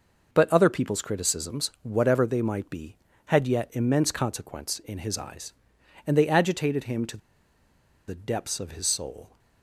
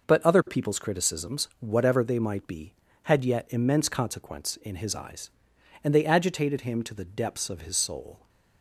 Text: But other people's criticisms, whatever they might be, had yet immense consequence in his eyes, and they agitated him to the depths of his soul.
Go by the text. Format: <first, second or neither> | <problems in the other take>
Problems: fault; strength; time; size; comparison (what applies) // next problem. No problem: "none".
second | pauses between "to" and "the"; noticeable; at 7.1 s; 0.90 s long